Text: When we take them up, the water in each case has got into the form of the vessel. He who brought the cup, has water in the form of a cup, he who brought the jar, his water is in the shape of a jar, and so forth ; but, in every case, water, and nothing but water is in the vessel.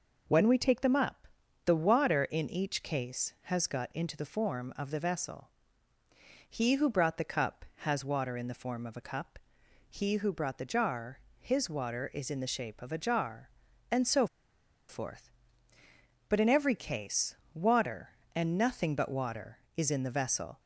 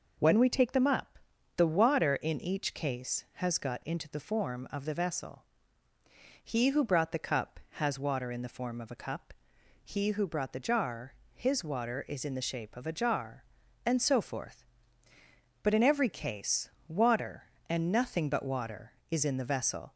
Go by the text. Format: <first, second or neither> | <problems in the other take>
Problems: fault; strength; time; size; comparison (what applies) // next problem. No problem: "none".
second | pauses between "so" and "forth"; noticeable; at 14.2 s; 0.63 s long